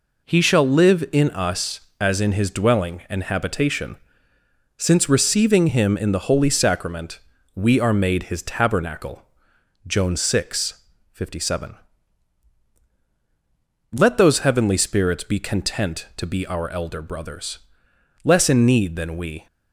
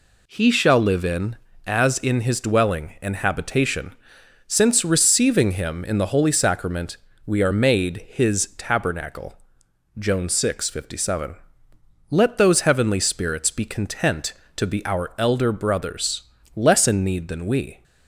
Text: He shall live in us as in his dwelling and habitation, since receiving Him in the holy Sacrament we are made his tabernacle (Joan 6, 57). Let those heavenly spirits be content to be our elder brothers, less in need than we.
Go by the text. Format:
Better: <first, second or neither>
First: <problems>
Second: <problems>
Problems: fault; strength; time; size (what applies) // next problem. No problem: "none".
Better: first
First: pauses between "Sacrament" and "we"; slight; at 7.2 s; 0.34 s long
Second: skips "us"; at 1.5 s // pauses between "Sacrament" and "we"; slight; at 6.9 s; 0.28 s long